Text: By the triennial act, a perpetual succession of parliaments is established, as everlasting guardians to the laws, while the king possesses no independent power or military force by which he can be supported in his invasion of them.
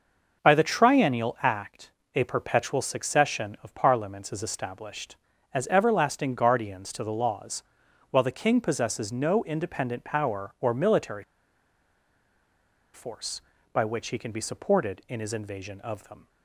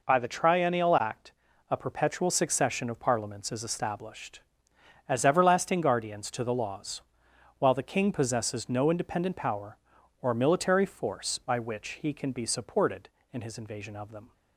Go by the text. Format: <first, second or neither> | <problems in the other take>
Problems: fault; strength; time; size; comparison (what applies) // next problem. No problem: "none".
second | starts louder than the rest; noticeable; until 1.4 s; 6 dB // pauses between "military" and "force"; strong; at 11.2 s; 1.7 s long